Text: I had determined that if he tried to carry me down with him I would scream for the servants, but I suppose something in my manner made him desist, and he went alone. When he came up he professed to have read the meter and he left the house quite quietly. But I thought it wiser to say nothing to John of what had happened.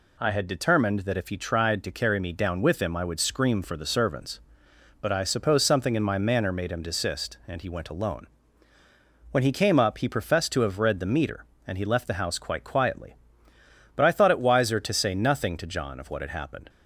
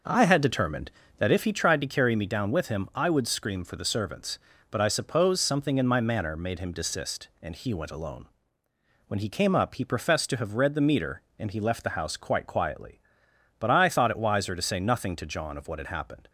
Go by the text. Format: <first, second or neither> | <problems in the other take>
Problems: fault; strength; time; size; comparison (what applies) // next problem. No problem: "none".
first | starts louder than the rest; noticeable; until 1.6 s; 5.5 dB